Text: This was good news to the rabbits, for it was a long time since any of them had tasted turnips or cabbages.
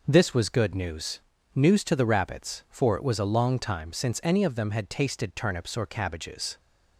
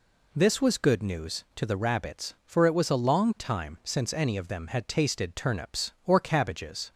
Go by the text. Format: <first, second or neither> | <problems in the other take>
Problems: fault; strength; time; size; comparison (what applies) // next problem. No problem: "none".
second | says "news" twice; at 1.5 s